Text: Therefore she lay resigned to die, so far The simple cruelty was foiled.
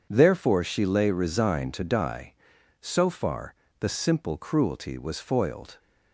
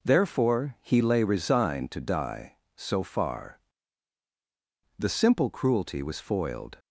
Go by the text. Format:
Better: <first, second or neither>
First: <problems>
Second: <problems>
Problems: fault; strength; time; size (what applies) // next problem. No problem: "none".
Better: first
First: pauses between "far" and "The"; slight; at 3.5 s; 0.24 s long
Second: says "he" for "she"; at 0.8 s // pauses between "far" and "The"; strong; at 3.5 s; 1.3 s long